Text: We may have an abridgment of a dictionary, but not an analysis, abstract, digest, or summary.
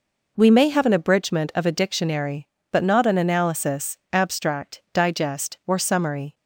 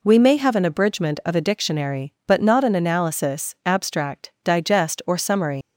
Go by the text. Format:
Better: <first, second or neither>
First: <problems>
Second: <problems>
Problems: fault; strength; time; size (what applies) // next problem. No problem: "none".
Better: first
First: none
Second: leaves "summary" unfinished; at 5.6 s; 125 ms